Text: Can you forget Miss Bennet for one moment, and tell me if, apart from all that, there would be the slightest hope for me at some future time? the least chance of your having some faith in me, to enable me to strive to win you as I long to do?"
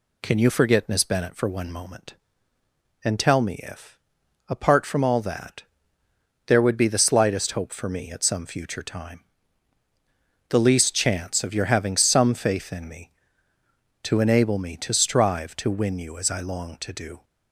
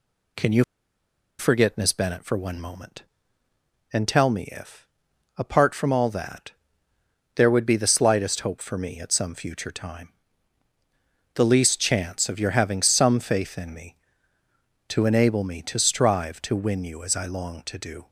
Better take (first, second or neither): first